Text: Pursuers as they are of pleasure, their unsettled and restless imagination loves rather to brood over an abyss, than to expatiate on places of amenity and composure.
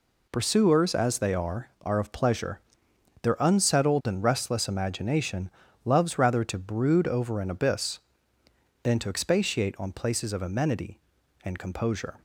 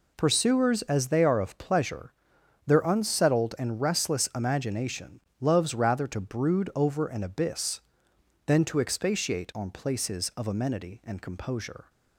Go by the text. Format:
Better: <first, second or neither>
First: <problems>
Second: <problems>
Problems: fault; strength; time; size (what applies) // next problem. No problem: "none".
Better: second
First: says "are" twice; at 1.8 s // pauses between "imagination" and "loves"; slight; at 5.4 s; 0.34 s long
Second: pauses between "imagination" and "loves"; slight; at 5.2 s; 0.20 s long